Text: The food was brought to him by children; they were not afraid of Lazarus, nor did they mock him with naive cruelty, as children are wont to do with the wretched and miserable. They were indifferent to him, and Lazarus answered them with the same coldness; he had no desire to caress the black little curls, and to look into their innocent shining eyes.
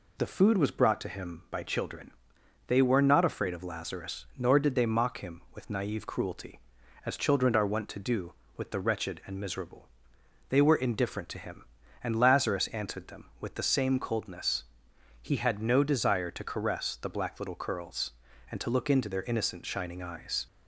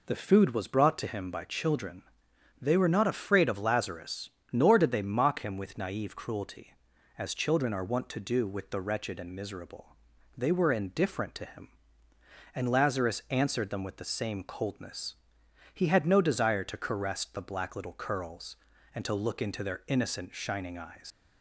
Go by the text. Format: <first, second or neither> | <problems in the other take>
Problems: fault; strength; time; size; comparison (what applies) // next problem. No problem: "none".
first | leaves "eyes" unfinished; at 21.1 s; 105 ms